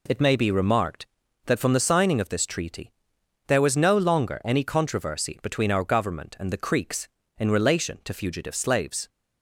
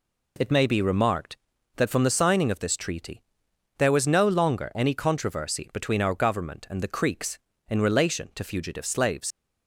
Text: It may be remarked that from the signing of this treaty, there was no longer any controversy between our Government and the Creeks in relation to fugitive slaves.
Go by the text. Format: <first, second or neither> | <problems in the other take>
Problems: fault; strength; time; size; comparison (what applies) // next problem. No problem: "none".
first | leaves "slaves" unfinished; at 9.3 s; 85 ms